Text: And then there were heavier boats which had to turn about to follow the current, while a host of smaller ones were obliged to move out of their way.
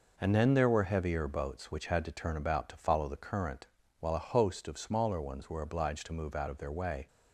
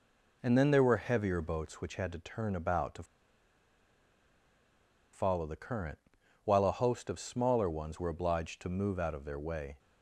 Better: first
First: none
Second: pauses between "to" and "follow"; strong; at 3.0 s; 2.1 s long

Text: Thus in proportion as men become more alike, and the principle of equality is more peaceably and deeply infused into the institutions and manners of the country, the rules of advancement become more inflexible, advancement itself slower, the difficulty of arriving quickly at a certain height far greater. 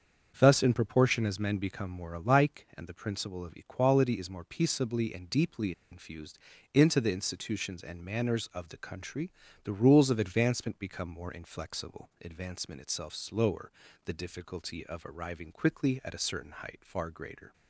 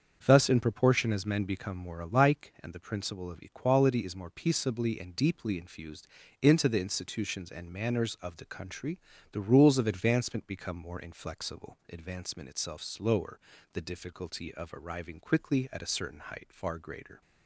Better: second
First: starts louder than the rest; until 1.3 s; 7 dB // pauses between "deeply" and "infused"; slight; at 5.7 s; 0.19 s long // pauses between "infused" and "into"; slight; at 6.3 s; 0.34 s long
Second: starts louder than the rest; until 1.2 s; 7 dB // pauses between "infused" and "into"; slight; at 6.0 s; 0.33 s long

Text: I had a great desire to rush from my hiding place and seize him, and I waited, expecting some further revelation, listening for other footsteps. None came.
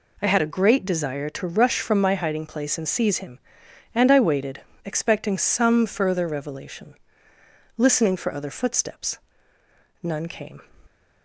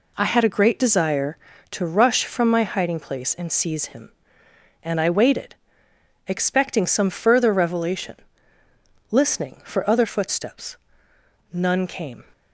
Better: neither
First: none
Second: none

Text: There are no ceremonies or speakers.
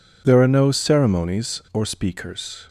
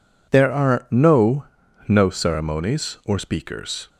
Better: first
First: none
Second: says "no" twice; at 1.8 s

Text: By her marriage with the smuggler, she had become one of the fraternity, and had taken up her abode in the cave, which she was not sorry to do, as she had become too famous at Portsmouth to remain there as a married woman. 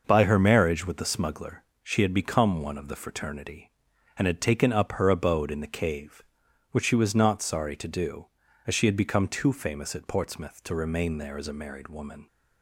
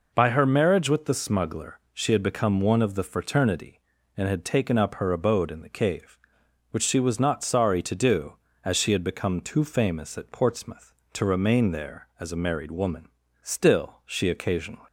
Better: first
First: none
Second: goes on to say "Still she occasionally"; from 13.4 s on; 1.4 s long

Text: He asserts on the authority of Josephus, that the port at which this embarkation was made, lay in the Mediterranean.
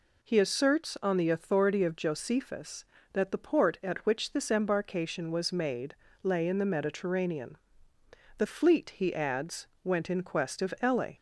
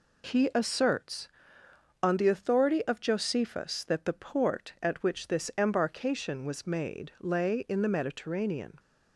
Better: second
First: goes on to say "The fleet he adds went in quest of ele"; strong; from 8.3 s on; 2.7 s long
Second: none

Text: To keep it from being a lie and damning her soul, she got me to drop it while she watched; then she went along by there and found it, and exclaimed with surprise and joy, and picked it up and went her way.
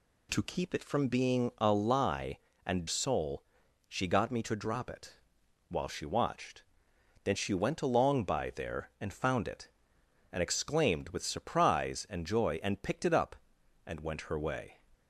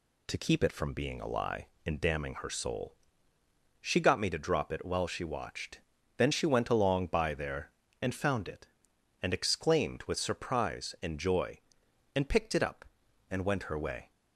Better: second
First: skips "damning her"; at 2.8 s // pauses between "it" and "while"; noticeable; at 5.1 s; 0.50 s long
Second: none

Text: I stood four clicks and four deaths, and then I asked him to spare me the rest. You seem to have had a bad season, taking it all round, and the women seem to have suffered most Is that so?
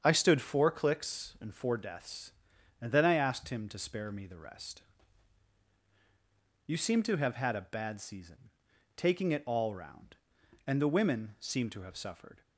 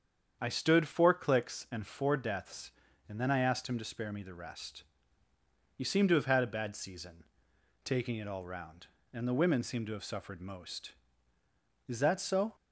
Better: second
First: starts louder than the rest; strong; until 1.0 s; 7.5 dB // stops before "most Is that so"; at 12.4 s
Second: starts louder than the rest; strong; until 1.4 s; 8 dB

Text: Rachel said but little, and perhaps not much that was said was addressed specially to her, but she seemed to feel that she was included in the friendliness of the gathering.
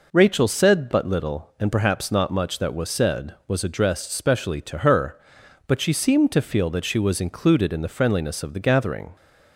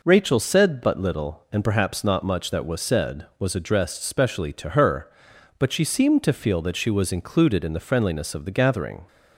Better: neither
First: none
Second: none

